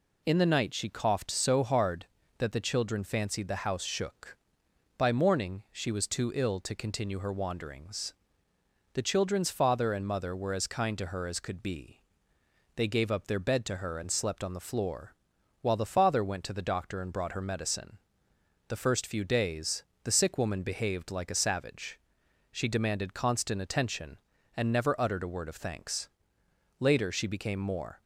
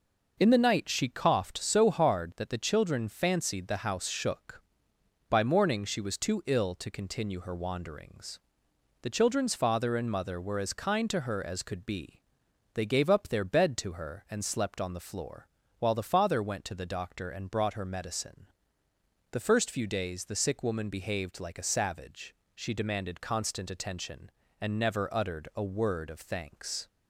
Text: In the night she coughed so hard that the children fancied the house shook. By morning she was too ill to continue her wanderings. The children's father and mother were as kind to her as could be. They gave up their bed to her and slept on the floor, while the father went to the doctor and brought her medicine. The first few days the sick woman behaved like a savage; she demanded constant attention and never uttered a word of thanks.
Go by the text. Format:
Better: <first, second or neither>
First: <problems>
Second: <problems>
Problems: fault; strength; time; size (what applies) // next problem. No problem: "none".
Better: second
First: pauses between "days" and "the"; slight; at 19.8 s; 0.20 s long // goes on to say "Later she became more"; noticeable; from 26.8 s on; 1.2 s long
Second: none